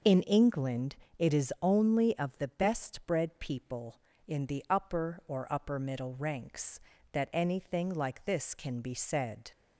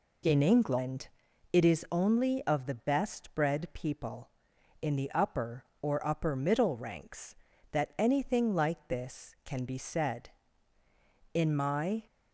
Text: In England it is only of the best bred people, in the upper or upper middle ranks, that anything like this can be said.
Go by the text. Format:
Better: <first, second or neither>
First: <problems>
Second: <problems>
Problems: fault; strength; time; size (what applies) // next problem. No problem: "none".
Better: first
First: pauses between "England" and "it"; slight; at 0.9 s; 0.20 s long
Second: pauses between "England" and "it"; at 1.0 s; 0.44 s long // goes on to say "In my"; noticeable; from 11.3 s on; 0.70 s long